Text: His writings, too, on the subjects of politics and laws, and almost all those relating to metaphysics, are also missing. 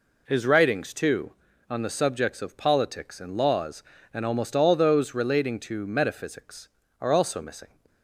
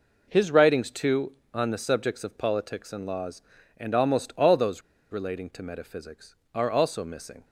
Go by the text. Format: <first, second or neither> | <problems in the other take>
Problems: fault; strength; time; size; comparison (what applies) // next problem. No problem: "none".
first | pauses between "those" and "relating"; slight; at 4.8 s; 0.31 s long